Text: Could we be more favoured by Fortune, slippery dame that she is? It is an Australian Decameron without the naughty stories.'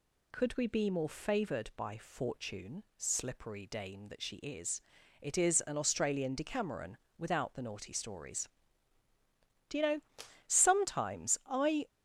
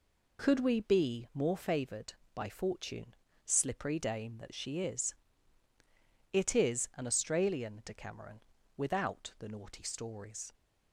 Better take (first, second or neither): second